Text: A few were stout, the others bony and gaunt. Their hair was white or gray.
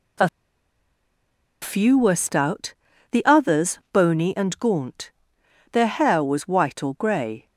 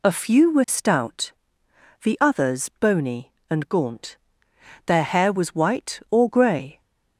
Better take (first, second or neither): second